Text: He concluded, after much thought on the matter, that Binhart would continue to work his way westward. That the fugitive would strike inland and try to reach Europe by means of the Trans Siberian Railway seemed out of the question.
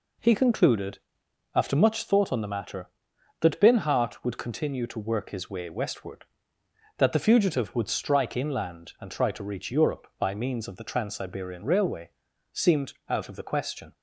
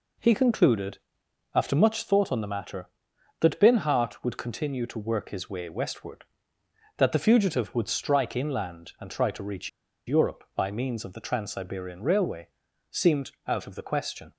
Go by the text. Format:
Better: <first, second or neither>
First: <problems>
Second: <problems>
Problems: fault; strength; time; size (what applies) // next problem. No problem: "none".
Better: first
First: pauses between "Railway" and "seemed"; at 12.1 s; 0.42 s long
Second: pauses between "reach" and "Europe"; at 9.6 s; 0.38 s long // pauses between "Railway" and "seemed"; at 12.4 s; 0.42 s long